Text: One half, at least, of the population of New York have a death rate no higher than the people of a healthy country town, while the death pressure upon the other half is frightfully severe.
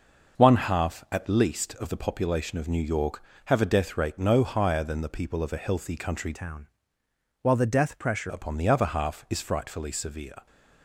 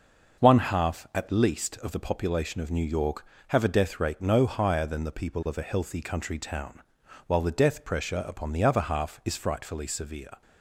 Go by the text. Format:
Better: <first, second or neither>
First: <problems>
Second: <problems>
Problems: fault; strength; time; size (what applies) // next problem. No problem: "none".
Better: second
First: changes voice from "town" to "pressure"; from 6.3 to 8.3 s; 2.0 s long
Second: none